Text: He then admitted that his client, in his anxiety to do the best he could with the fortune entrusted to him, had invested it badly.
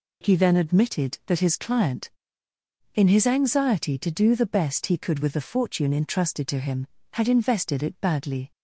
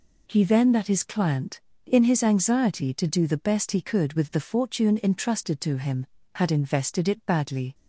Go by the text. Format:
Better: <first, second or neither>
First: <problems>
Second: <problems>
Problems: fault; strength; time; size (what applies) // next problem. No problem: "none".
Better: first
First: none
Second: skips "admitted"; at 0.7 s